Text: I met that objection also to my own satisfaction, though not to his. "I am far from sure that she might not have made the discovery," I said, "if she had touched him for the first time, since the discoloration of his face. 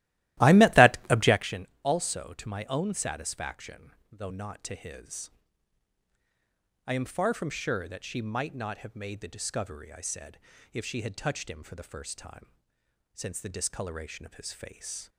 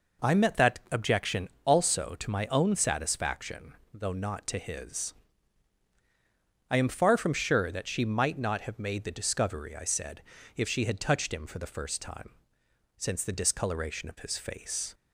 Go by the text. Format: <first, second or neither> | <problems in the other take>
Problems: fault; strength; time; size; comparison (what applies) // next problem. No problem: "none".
second | starts louder than the rest; strong; until 1.5 s; 16 dB // pauses between "objection" and "also"; slight; at 1.6 s; 0.16 s long; slight in the second